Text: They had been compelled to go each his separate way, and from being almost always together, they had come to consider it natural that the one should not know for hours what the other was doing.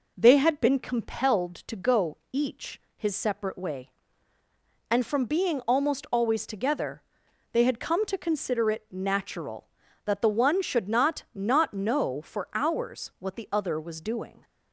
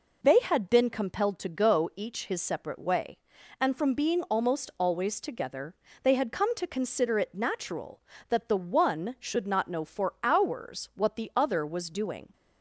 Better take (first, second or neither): second